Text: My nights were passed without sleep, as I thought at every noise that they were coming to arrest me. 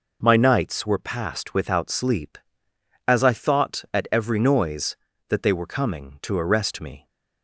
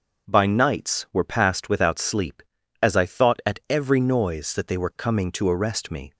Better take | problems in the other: first | says "By" for "My"; at 0.2 s

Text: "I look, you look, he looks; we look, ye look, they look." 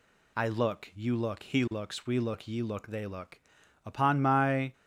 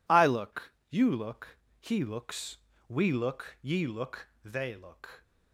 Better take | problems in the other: second | goes on to say "Upon my"; noticeable; from 3.8 s on; 0.86 s long

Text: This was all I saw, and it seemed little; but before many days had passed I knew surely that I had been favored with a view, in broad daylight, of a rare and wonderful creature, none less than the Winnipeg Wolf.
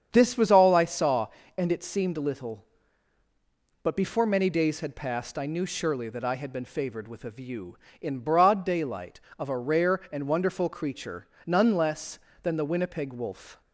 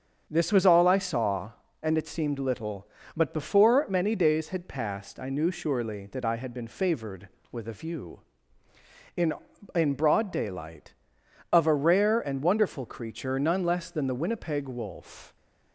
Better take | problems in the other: first | starts louder than the rest; until 1.3 s; 7 dB; strong in the first // says "in" twice; at 9.7 s

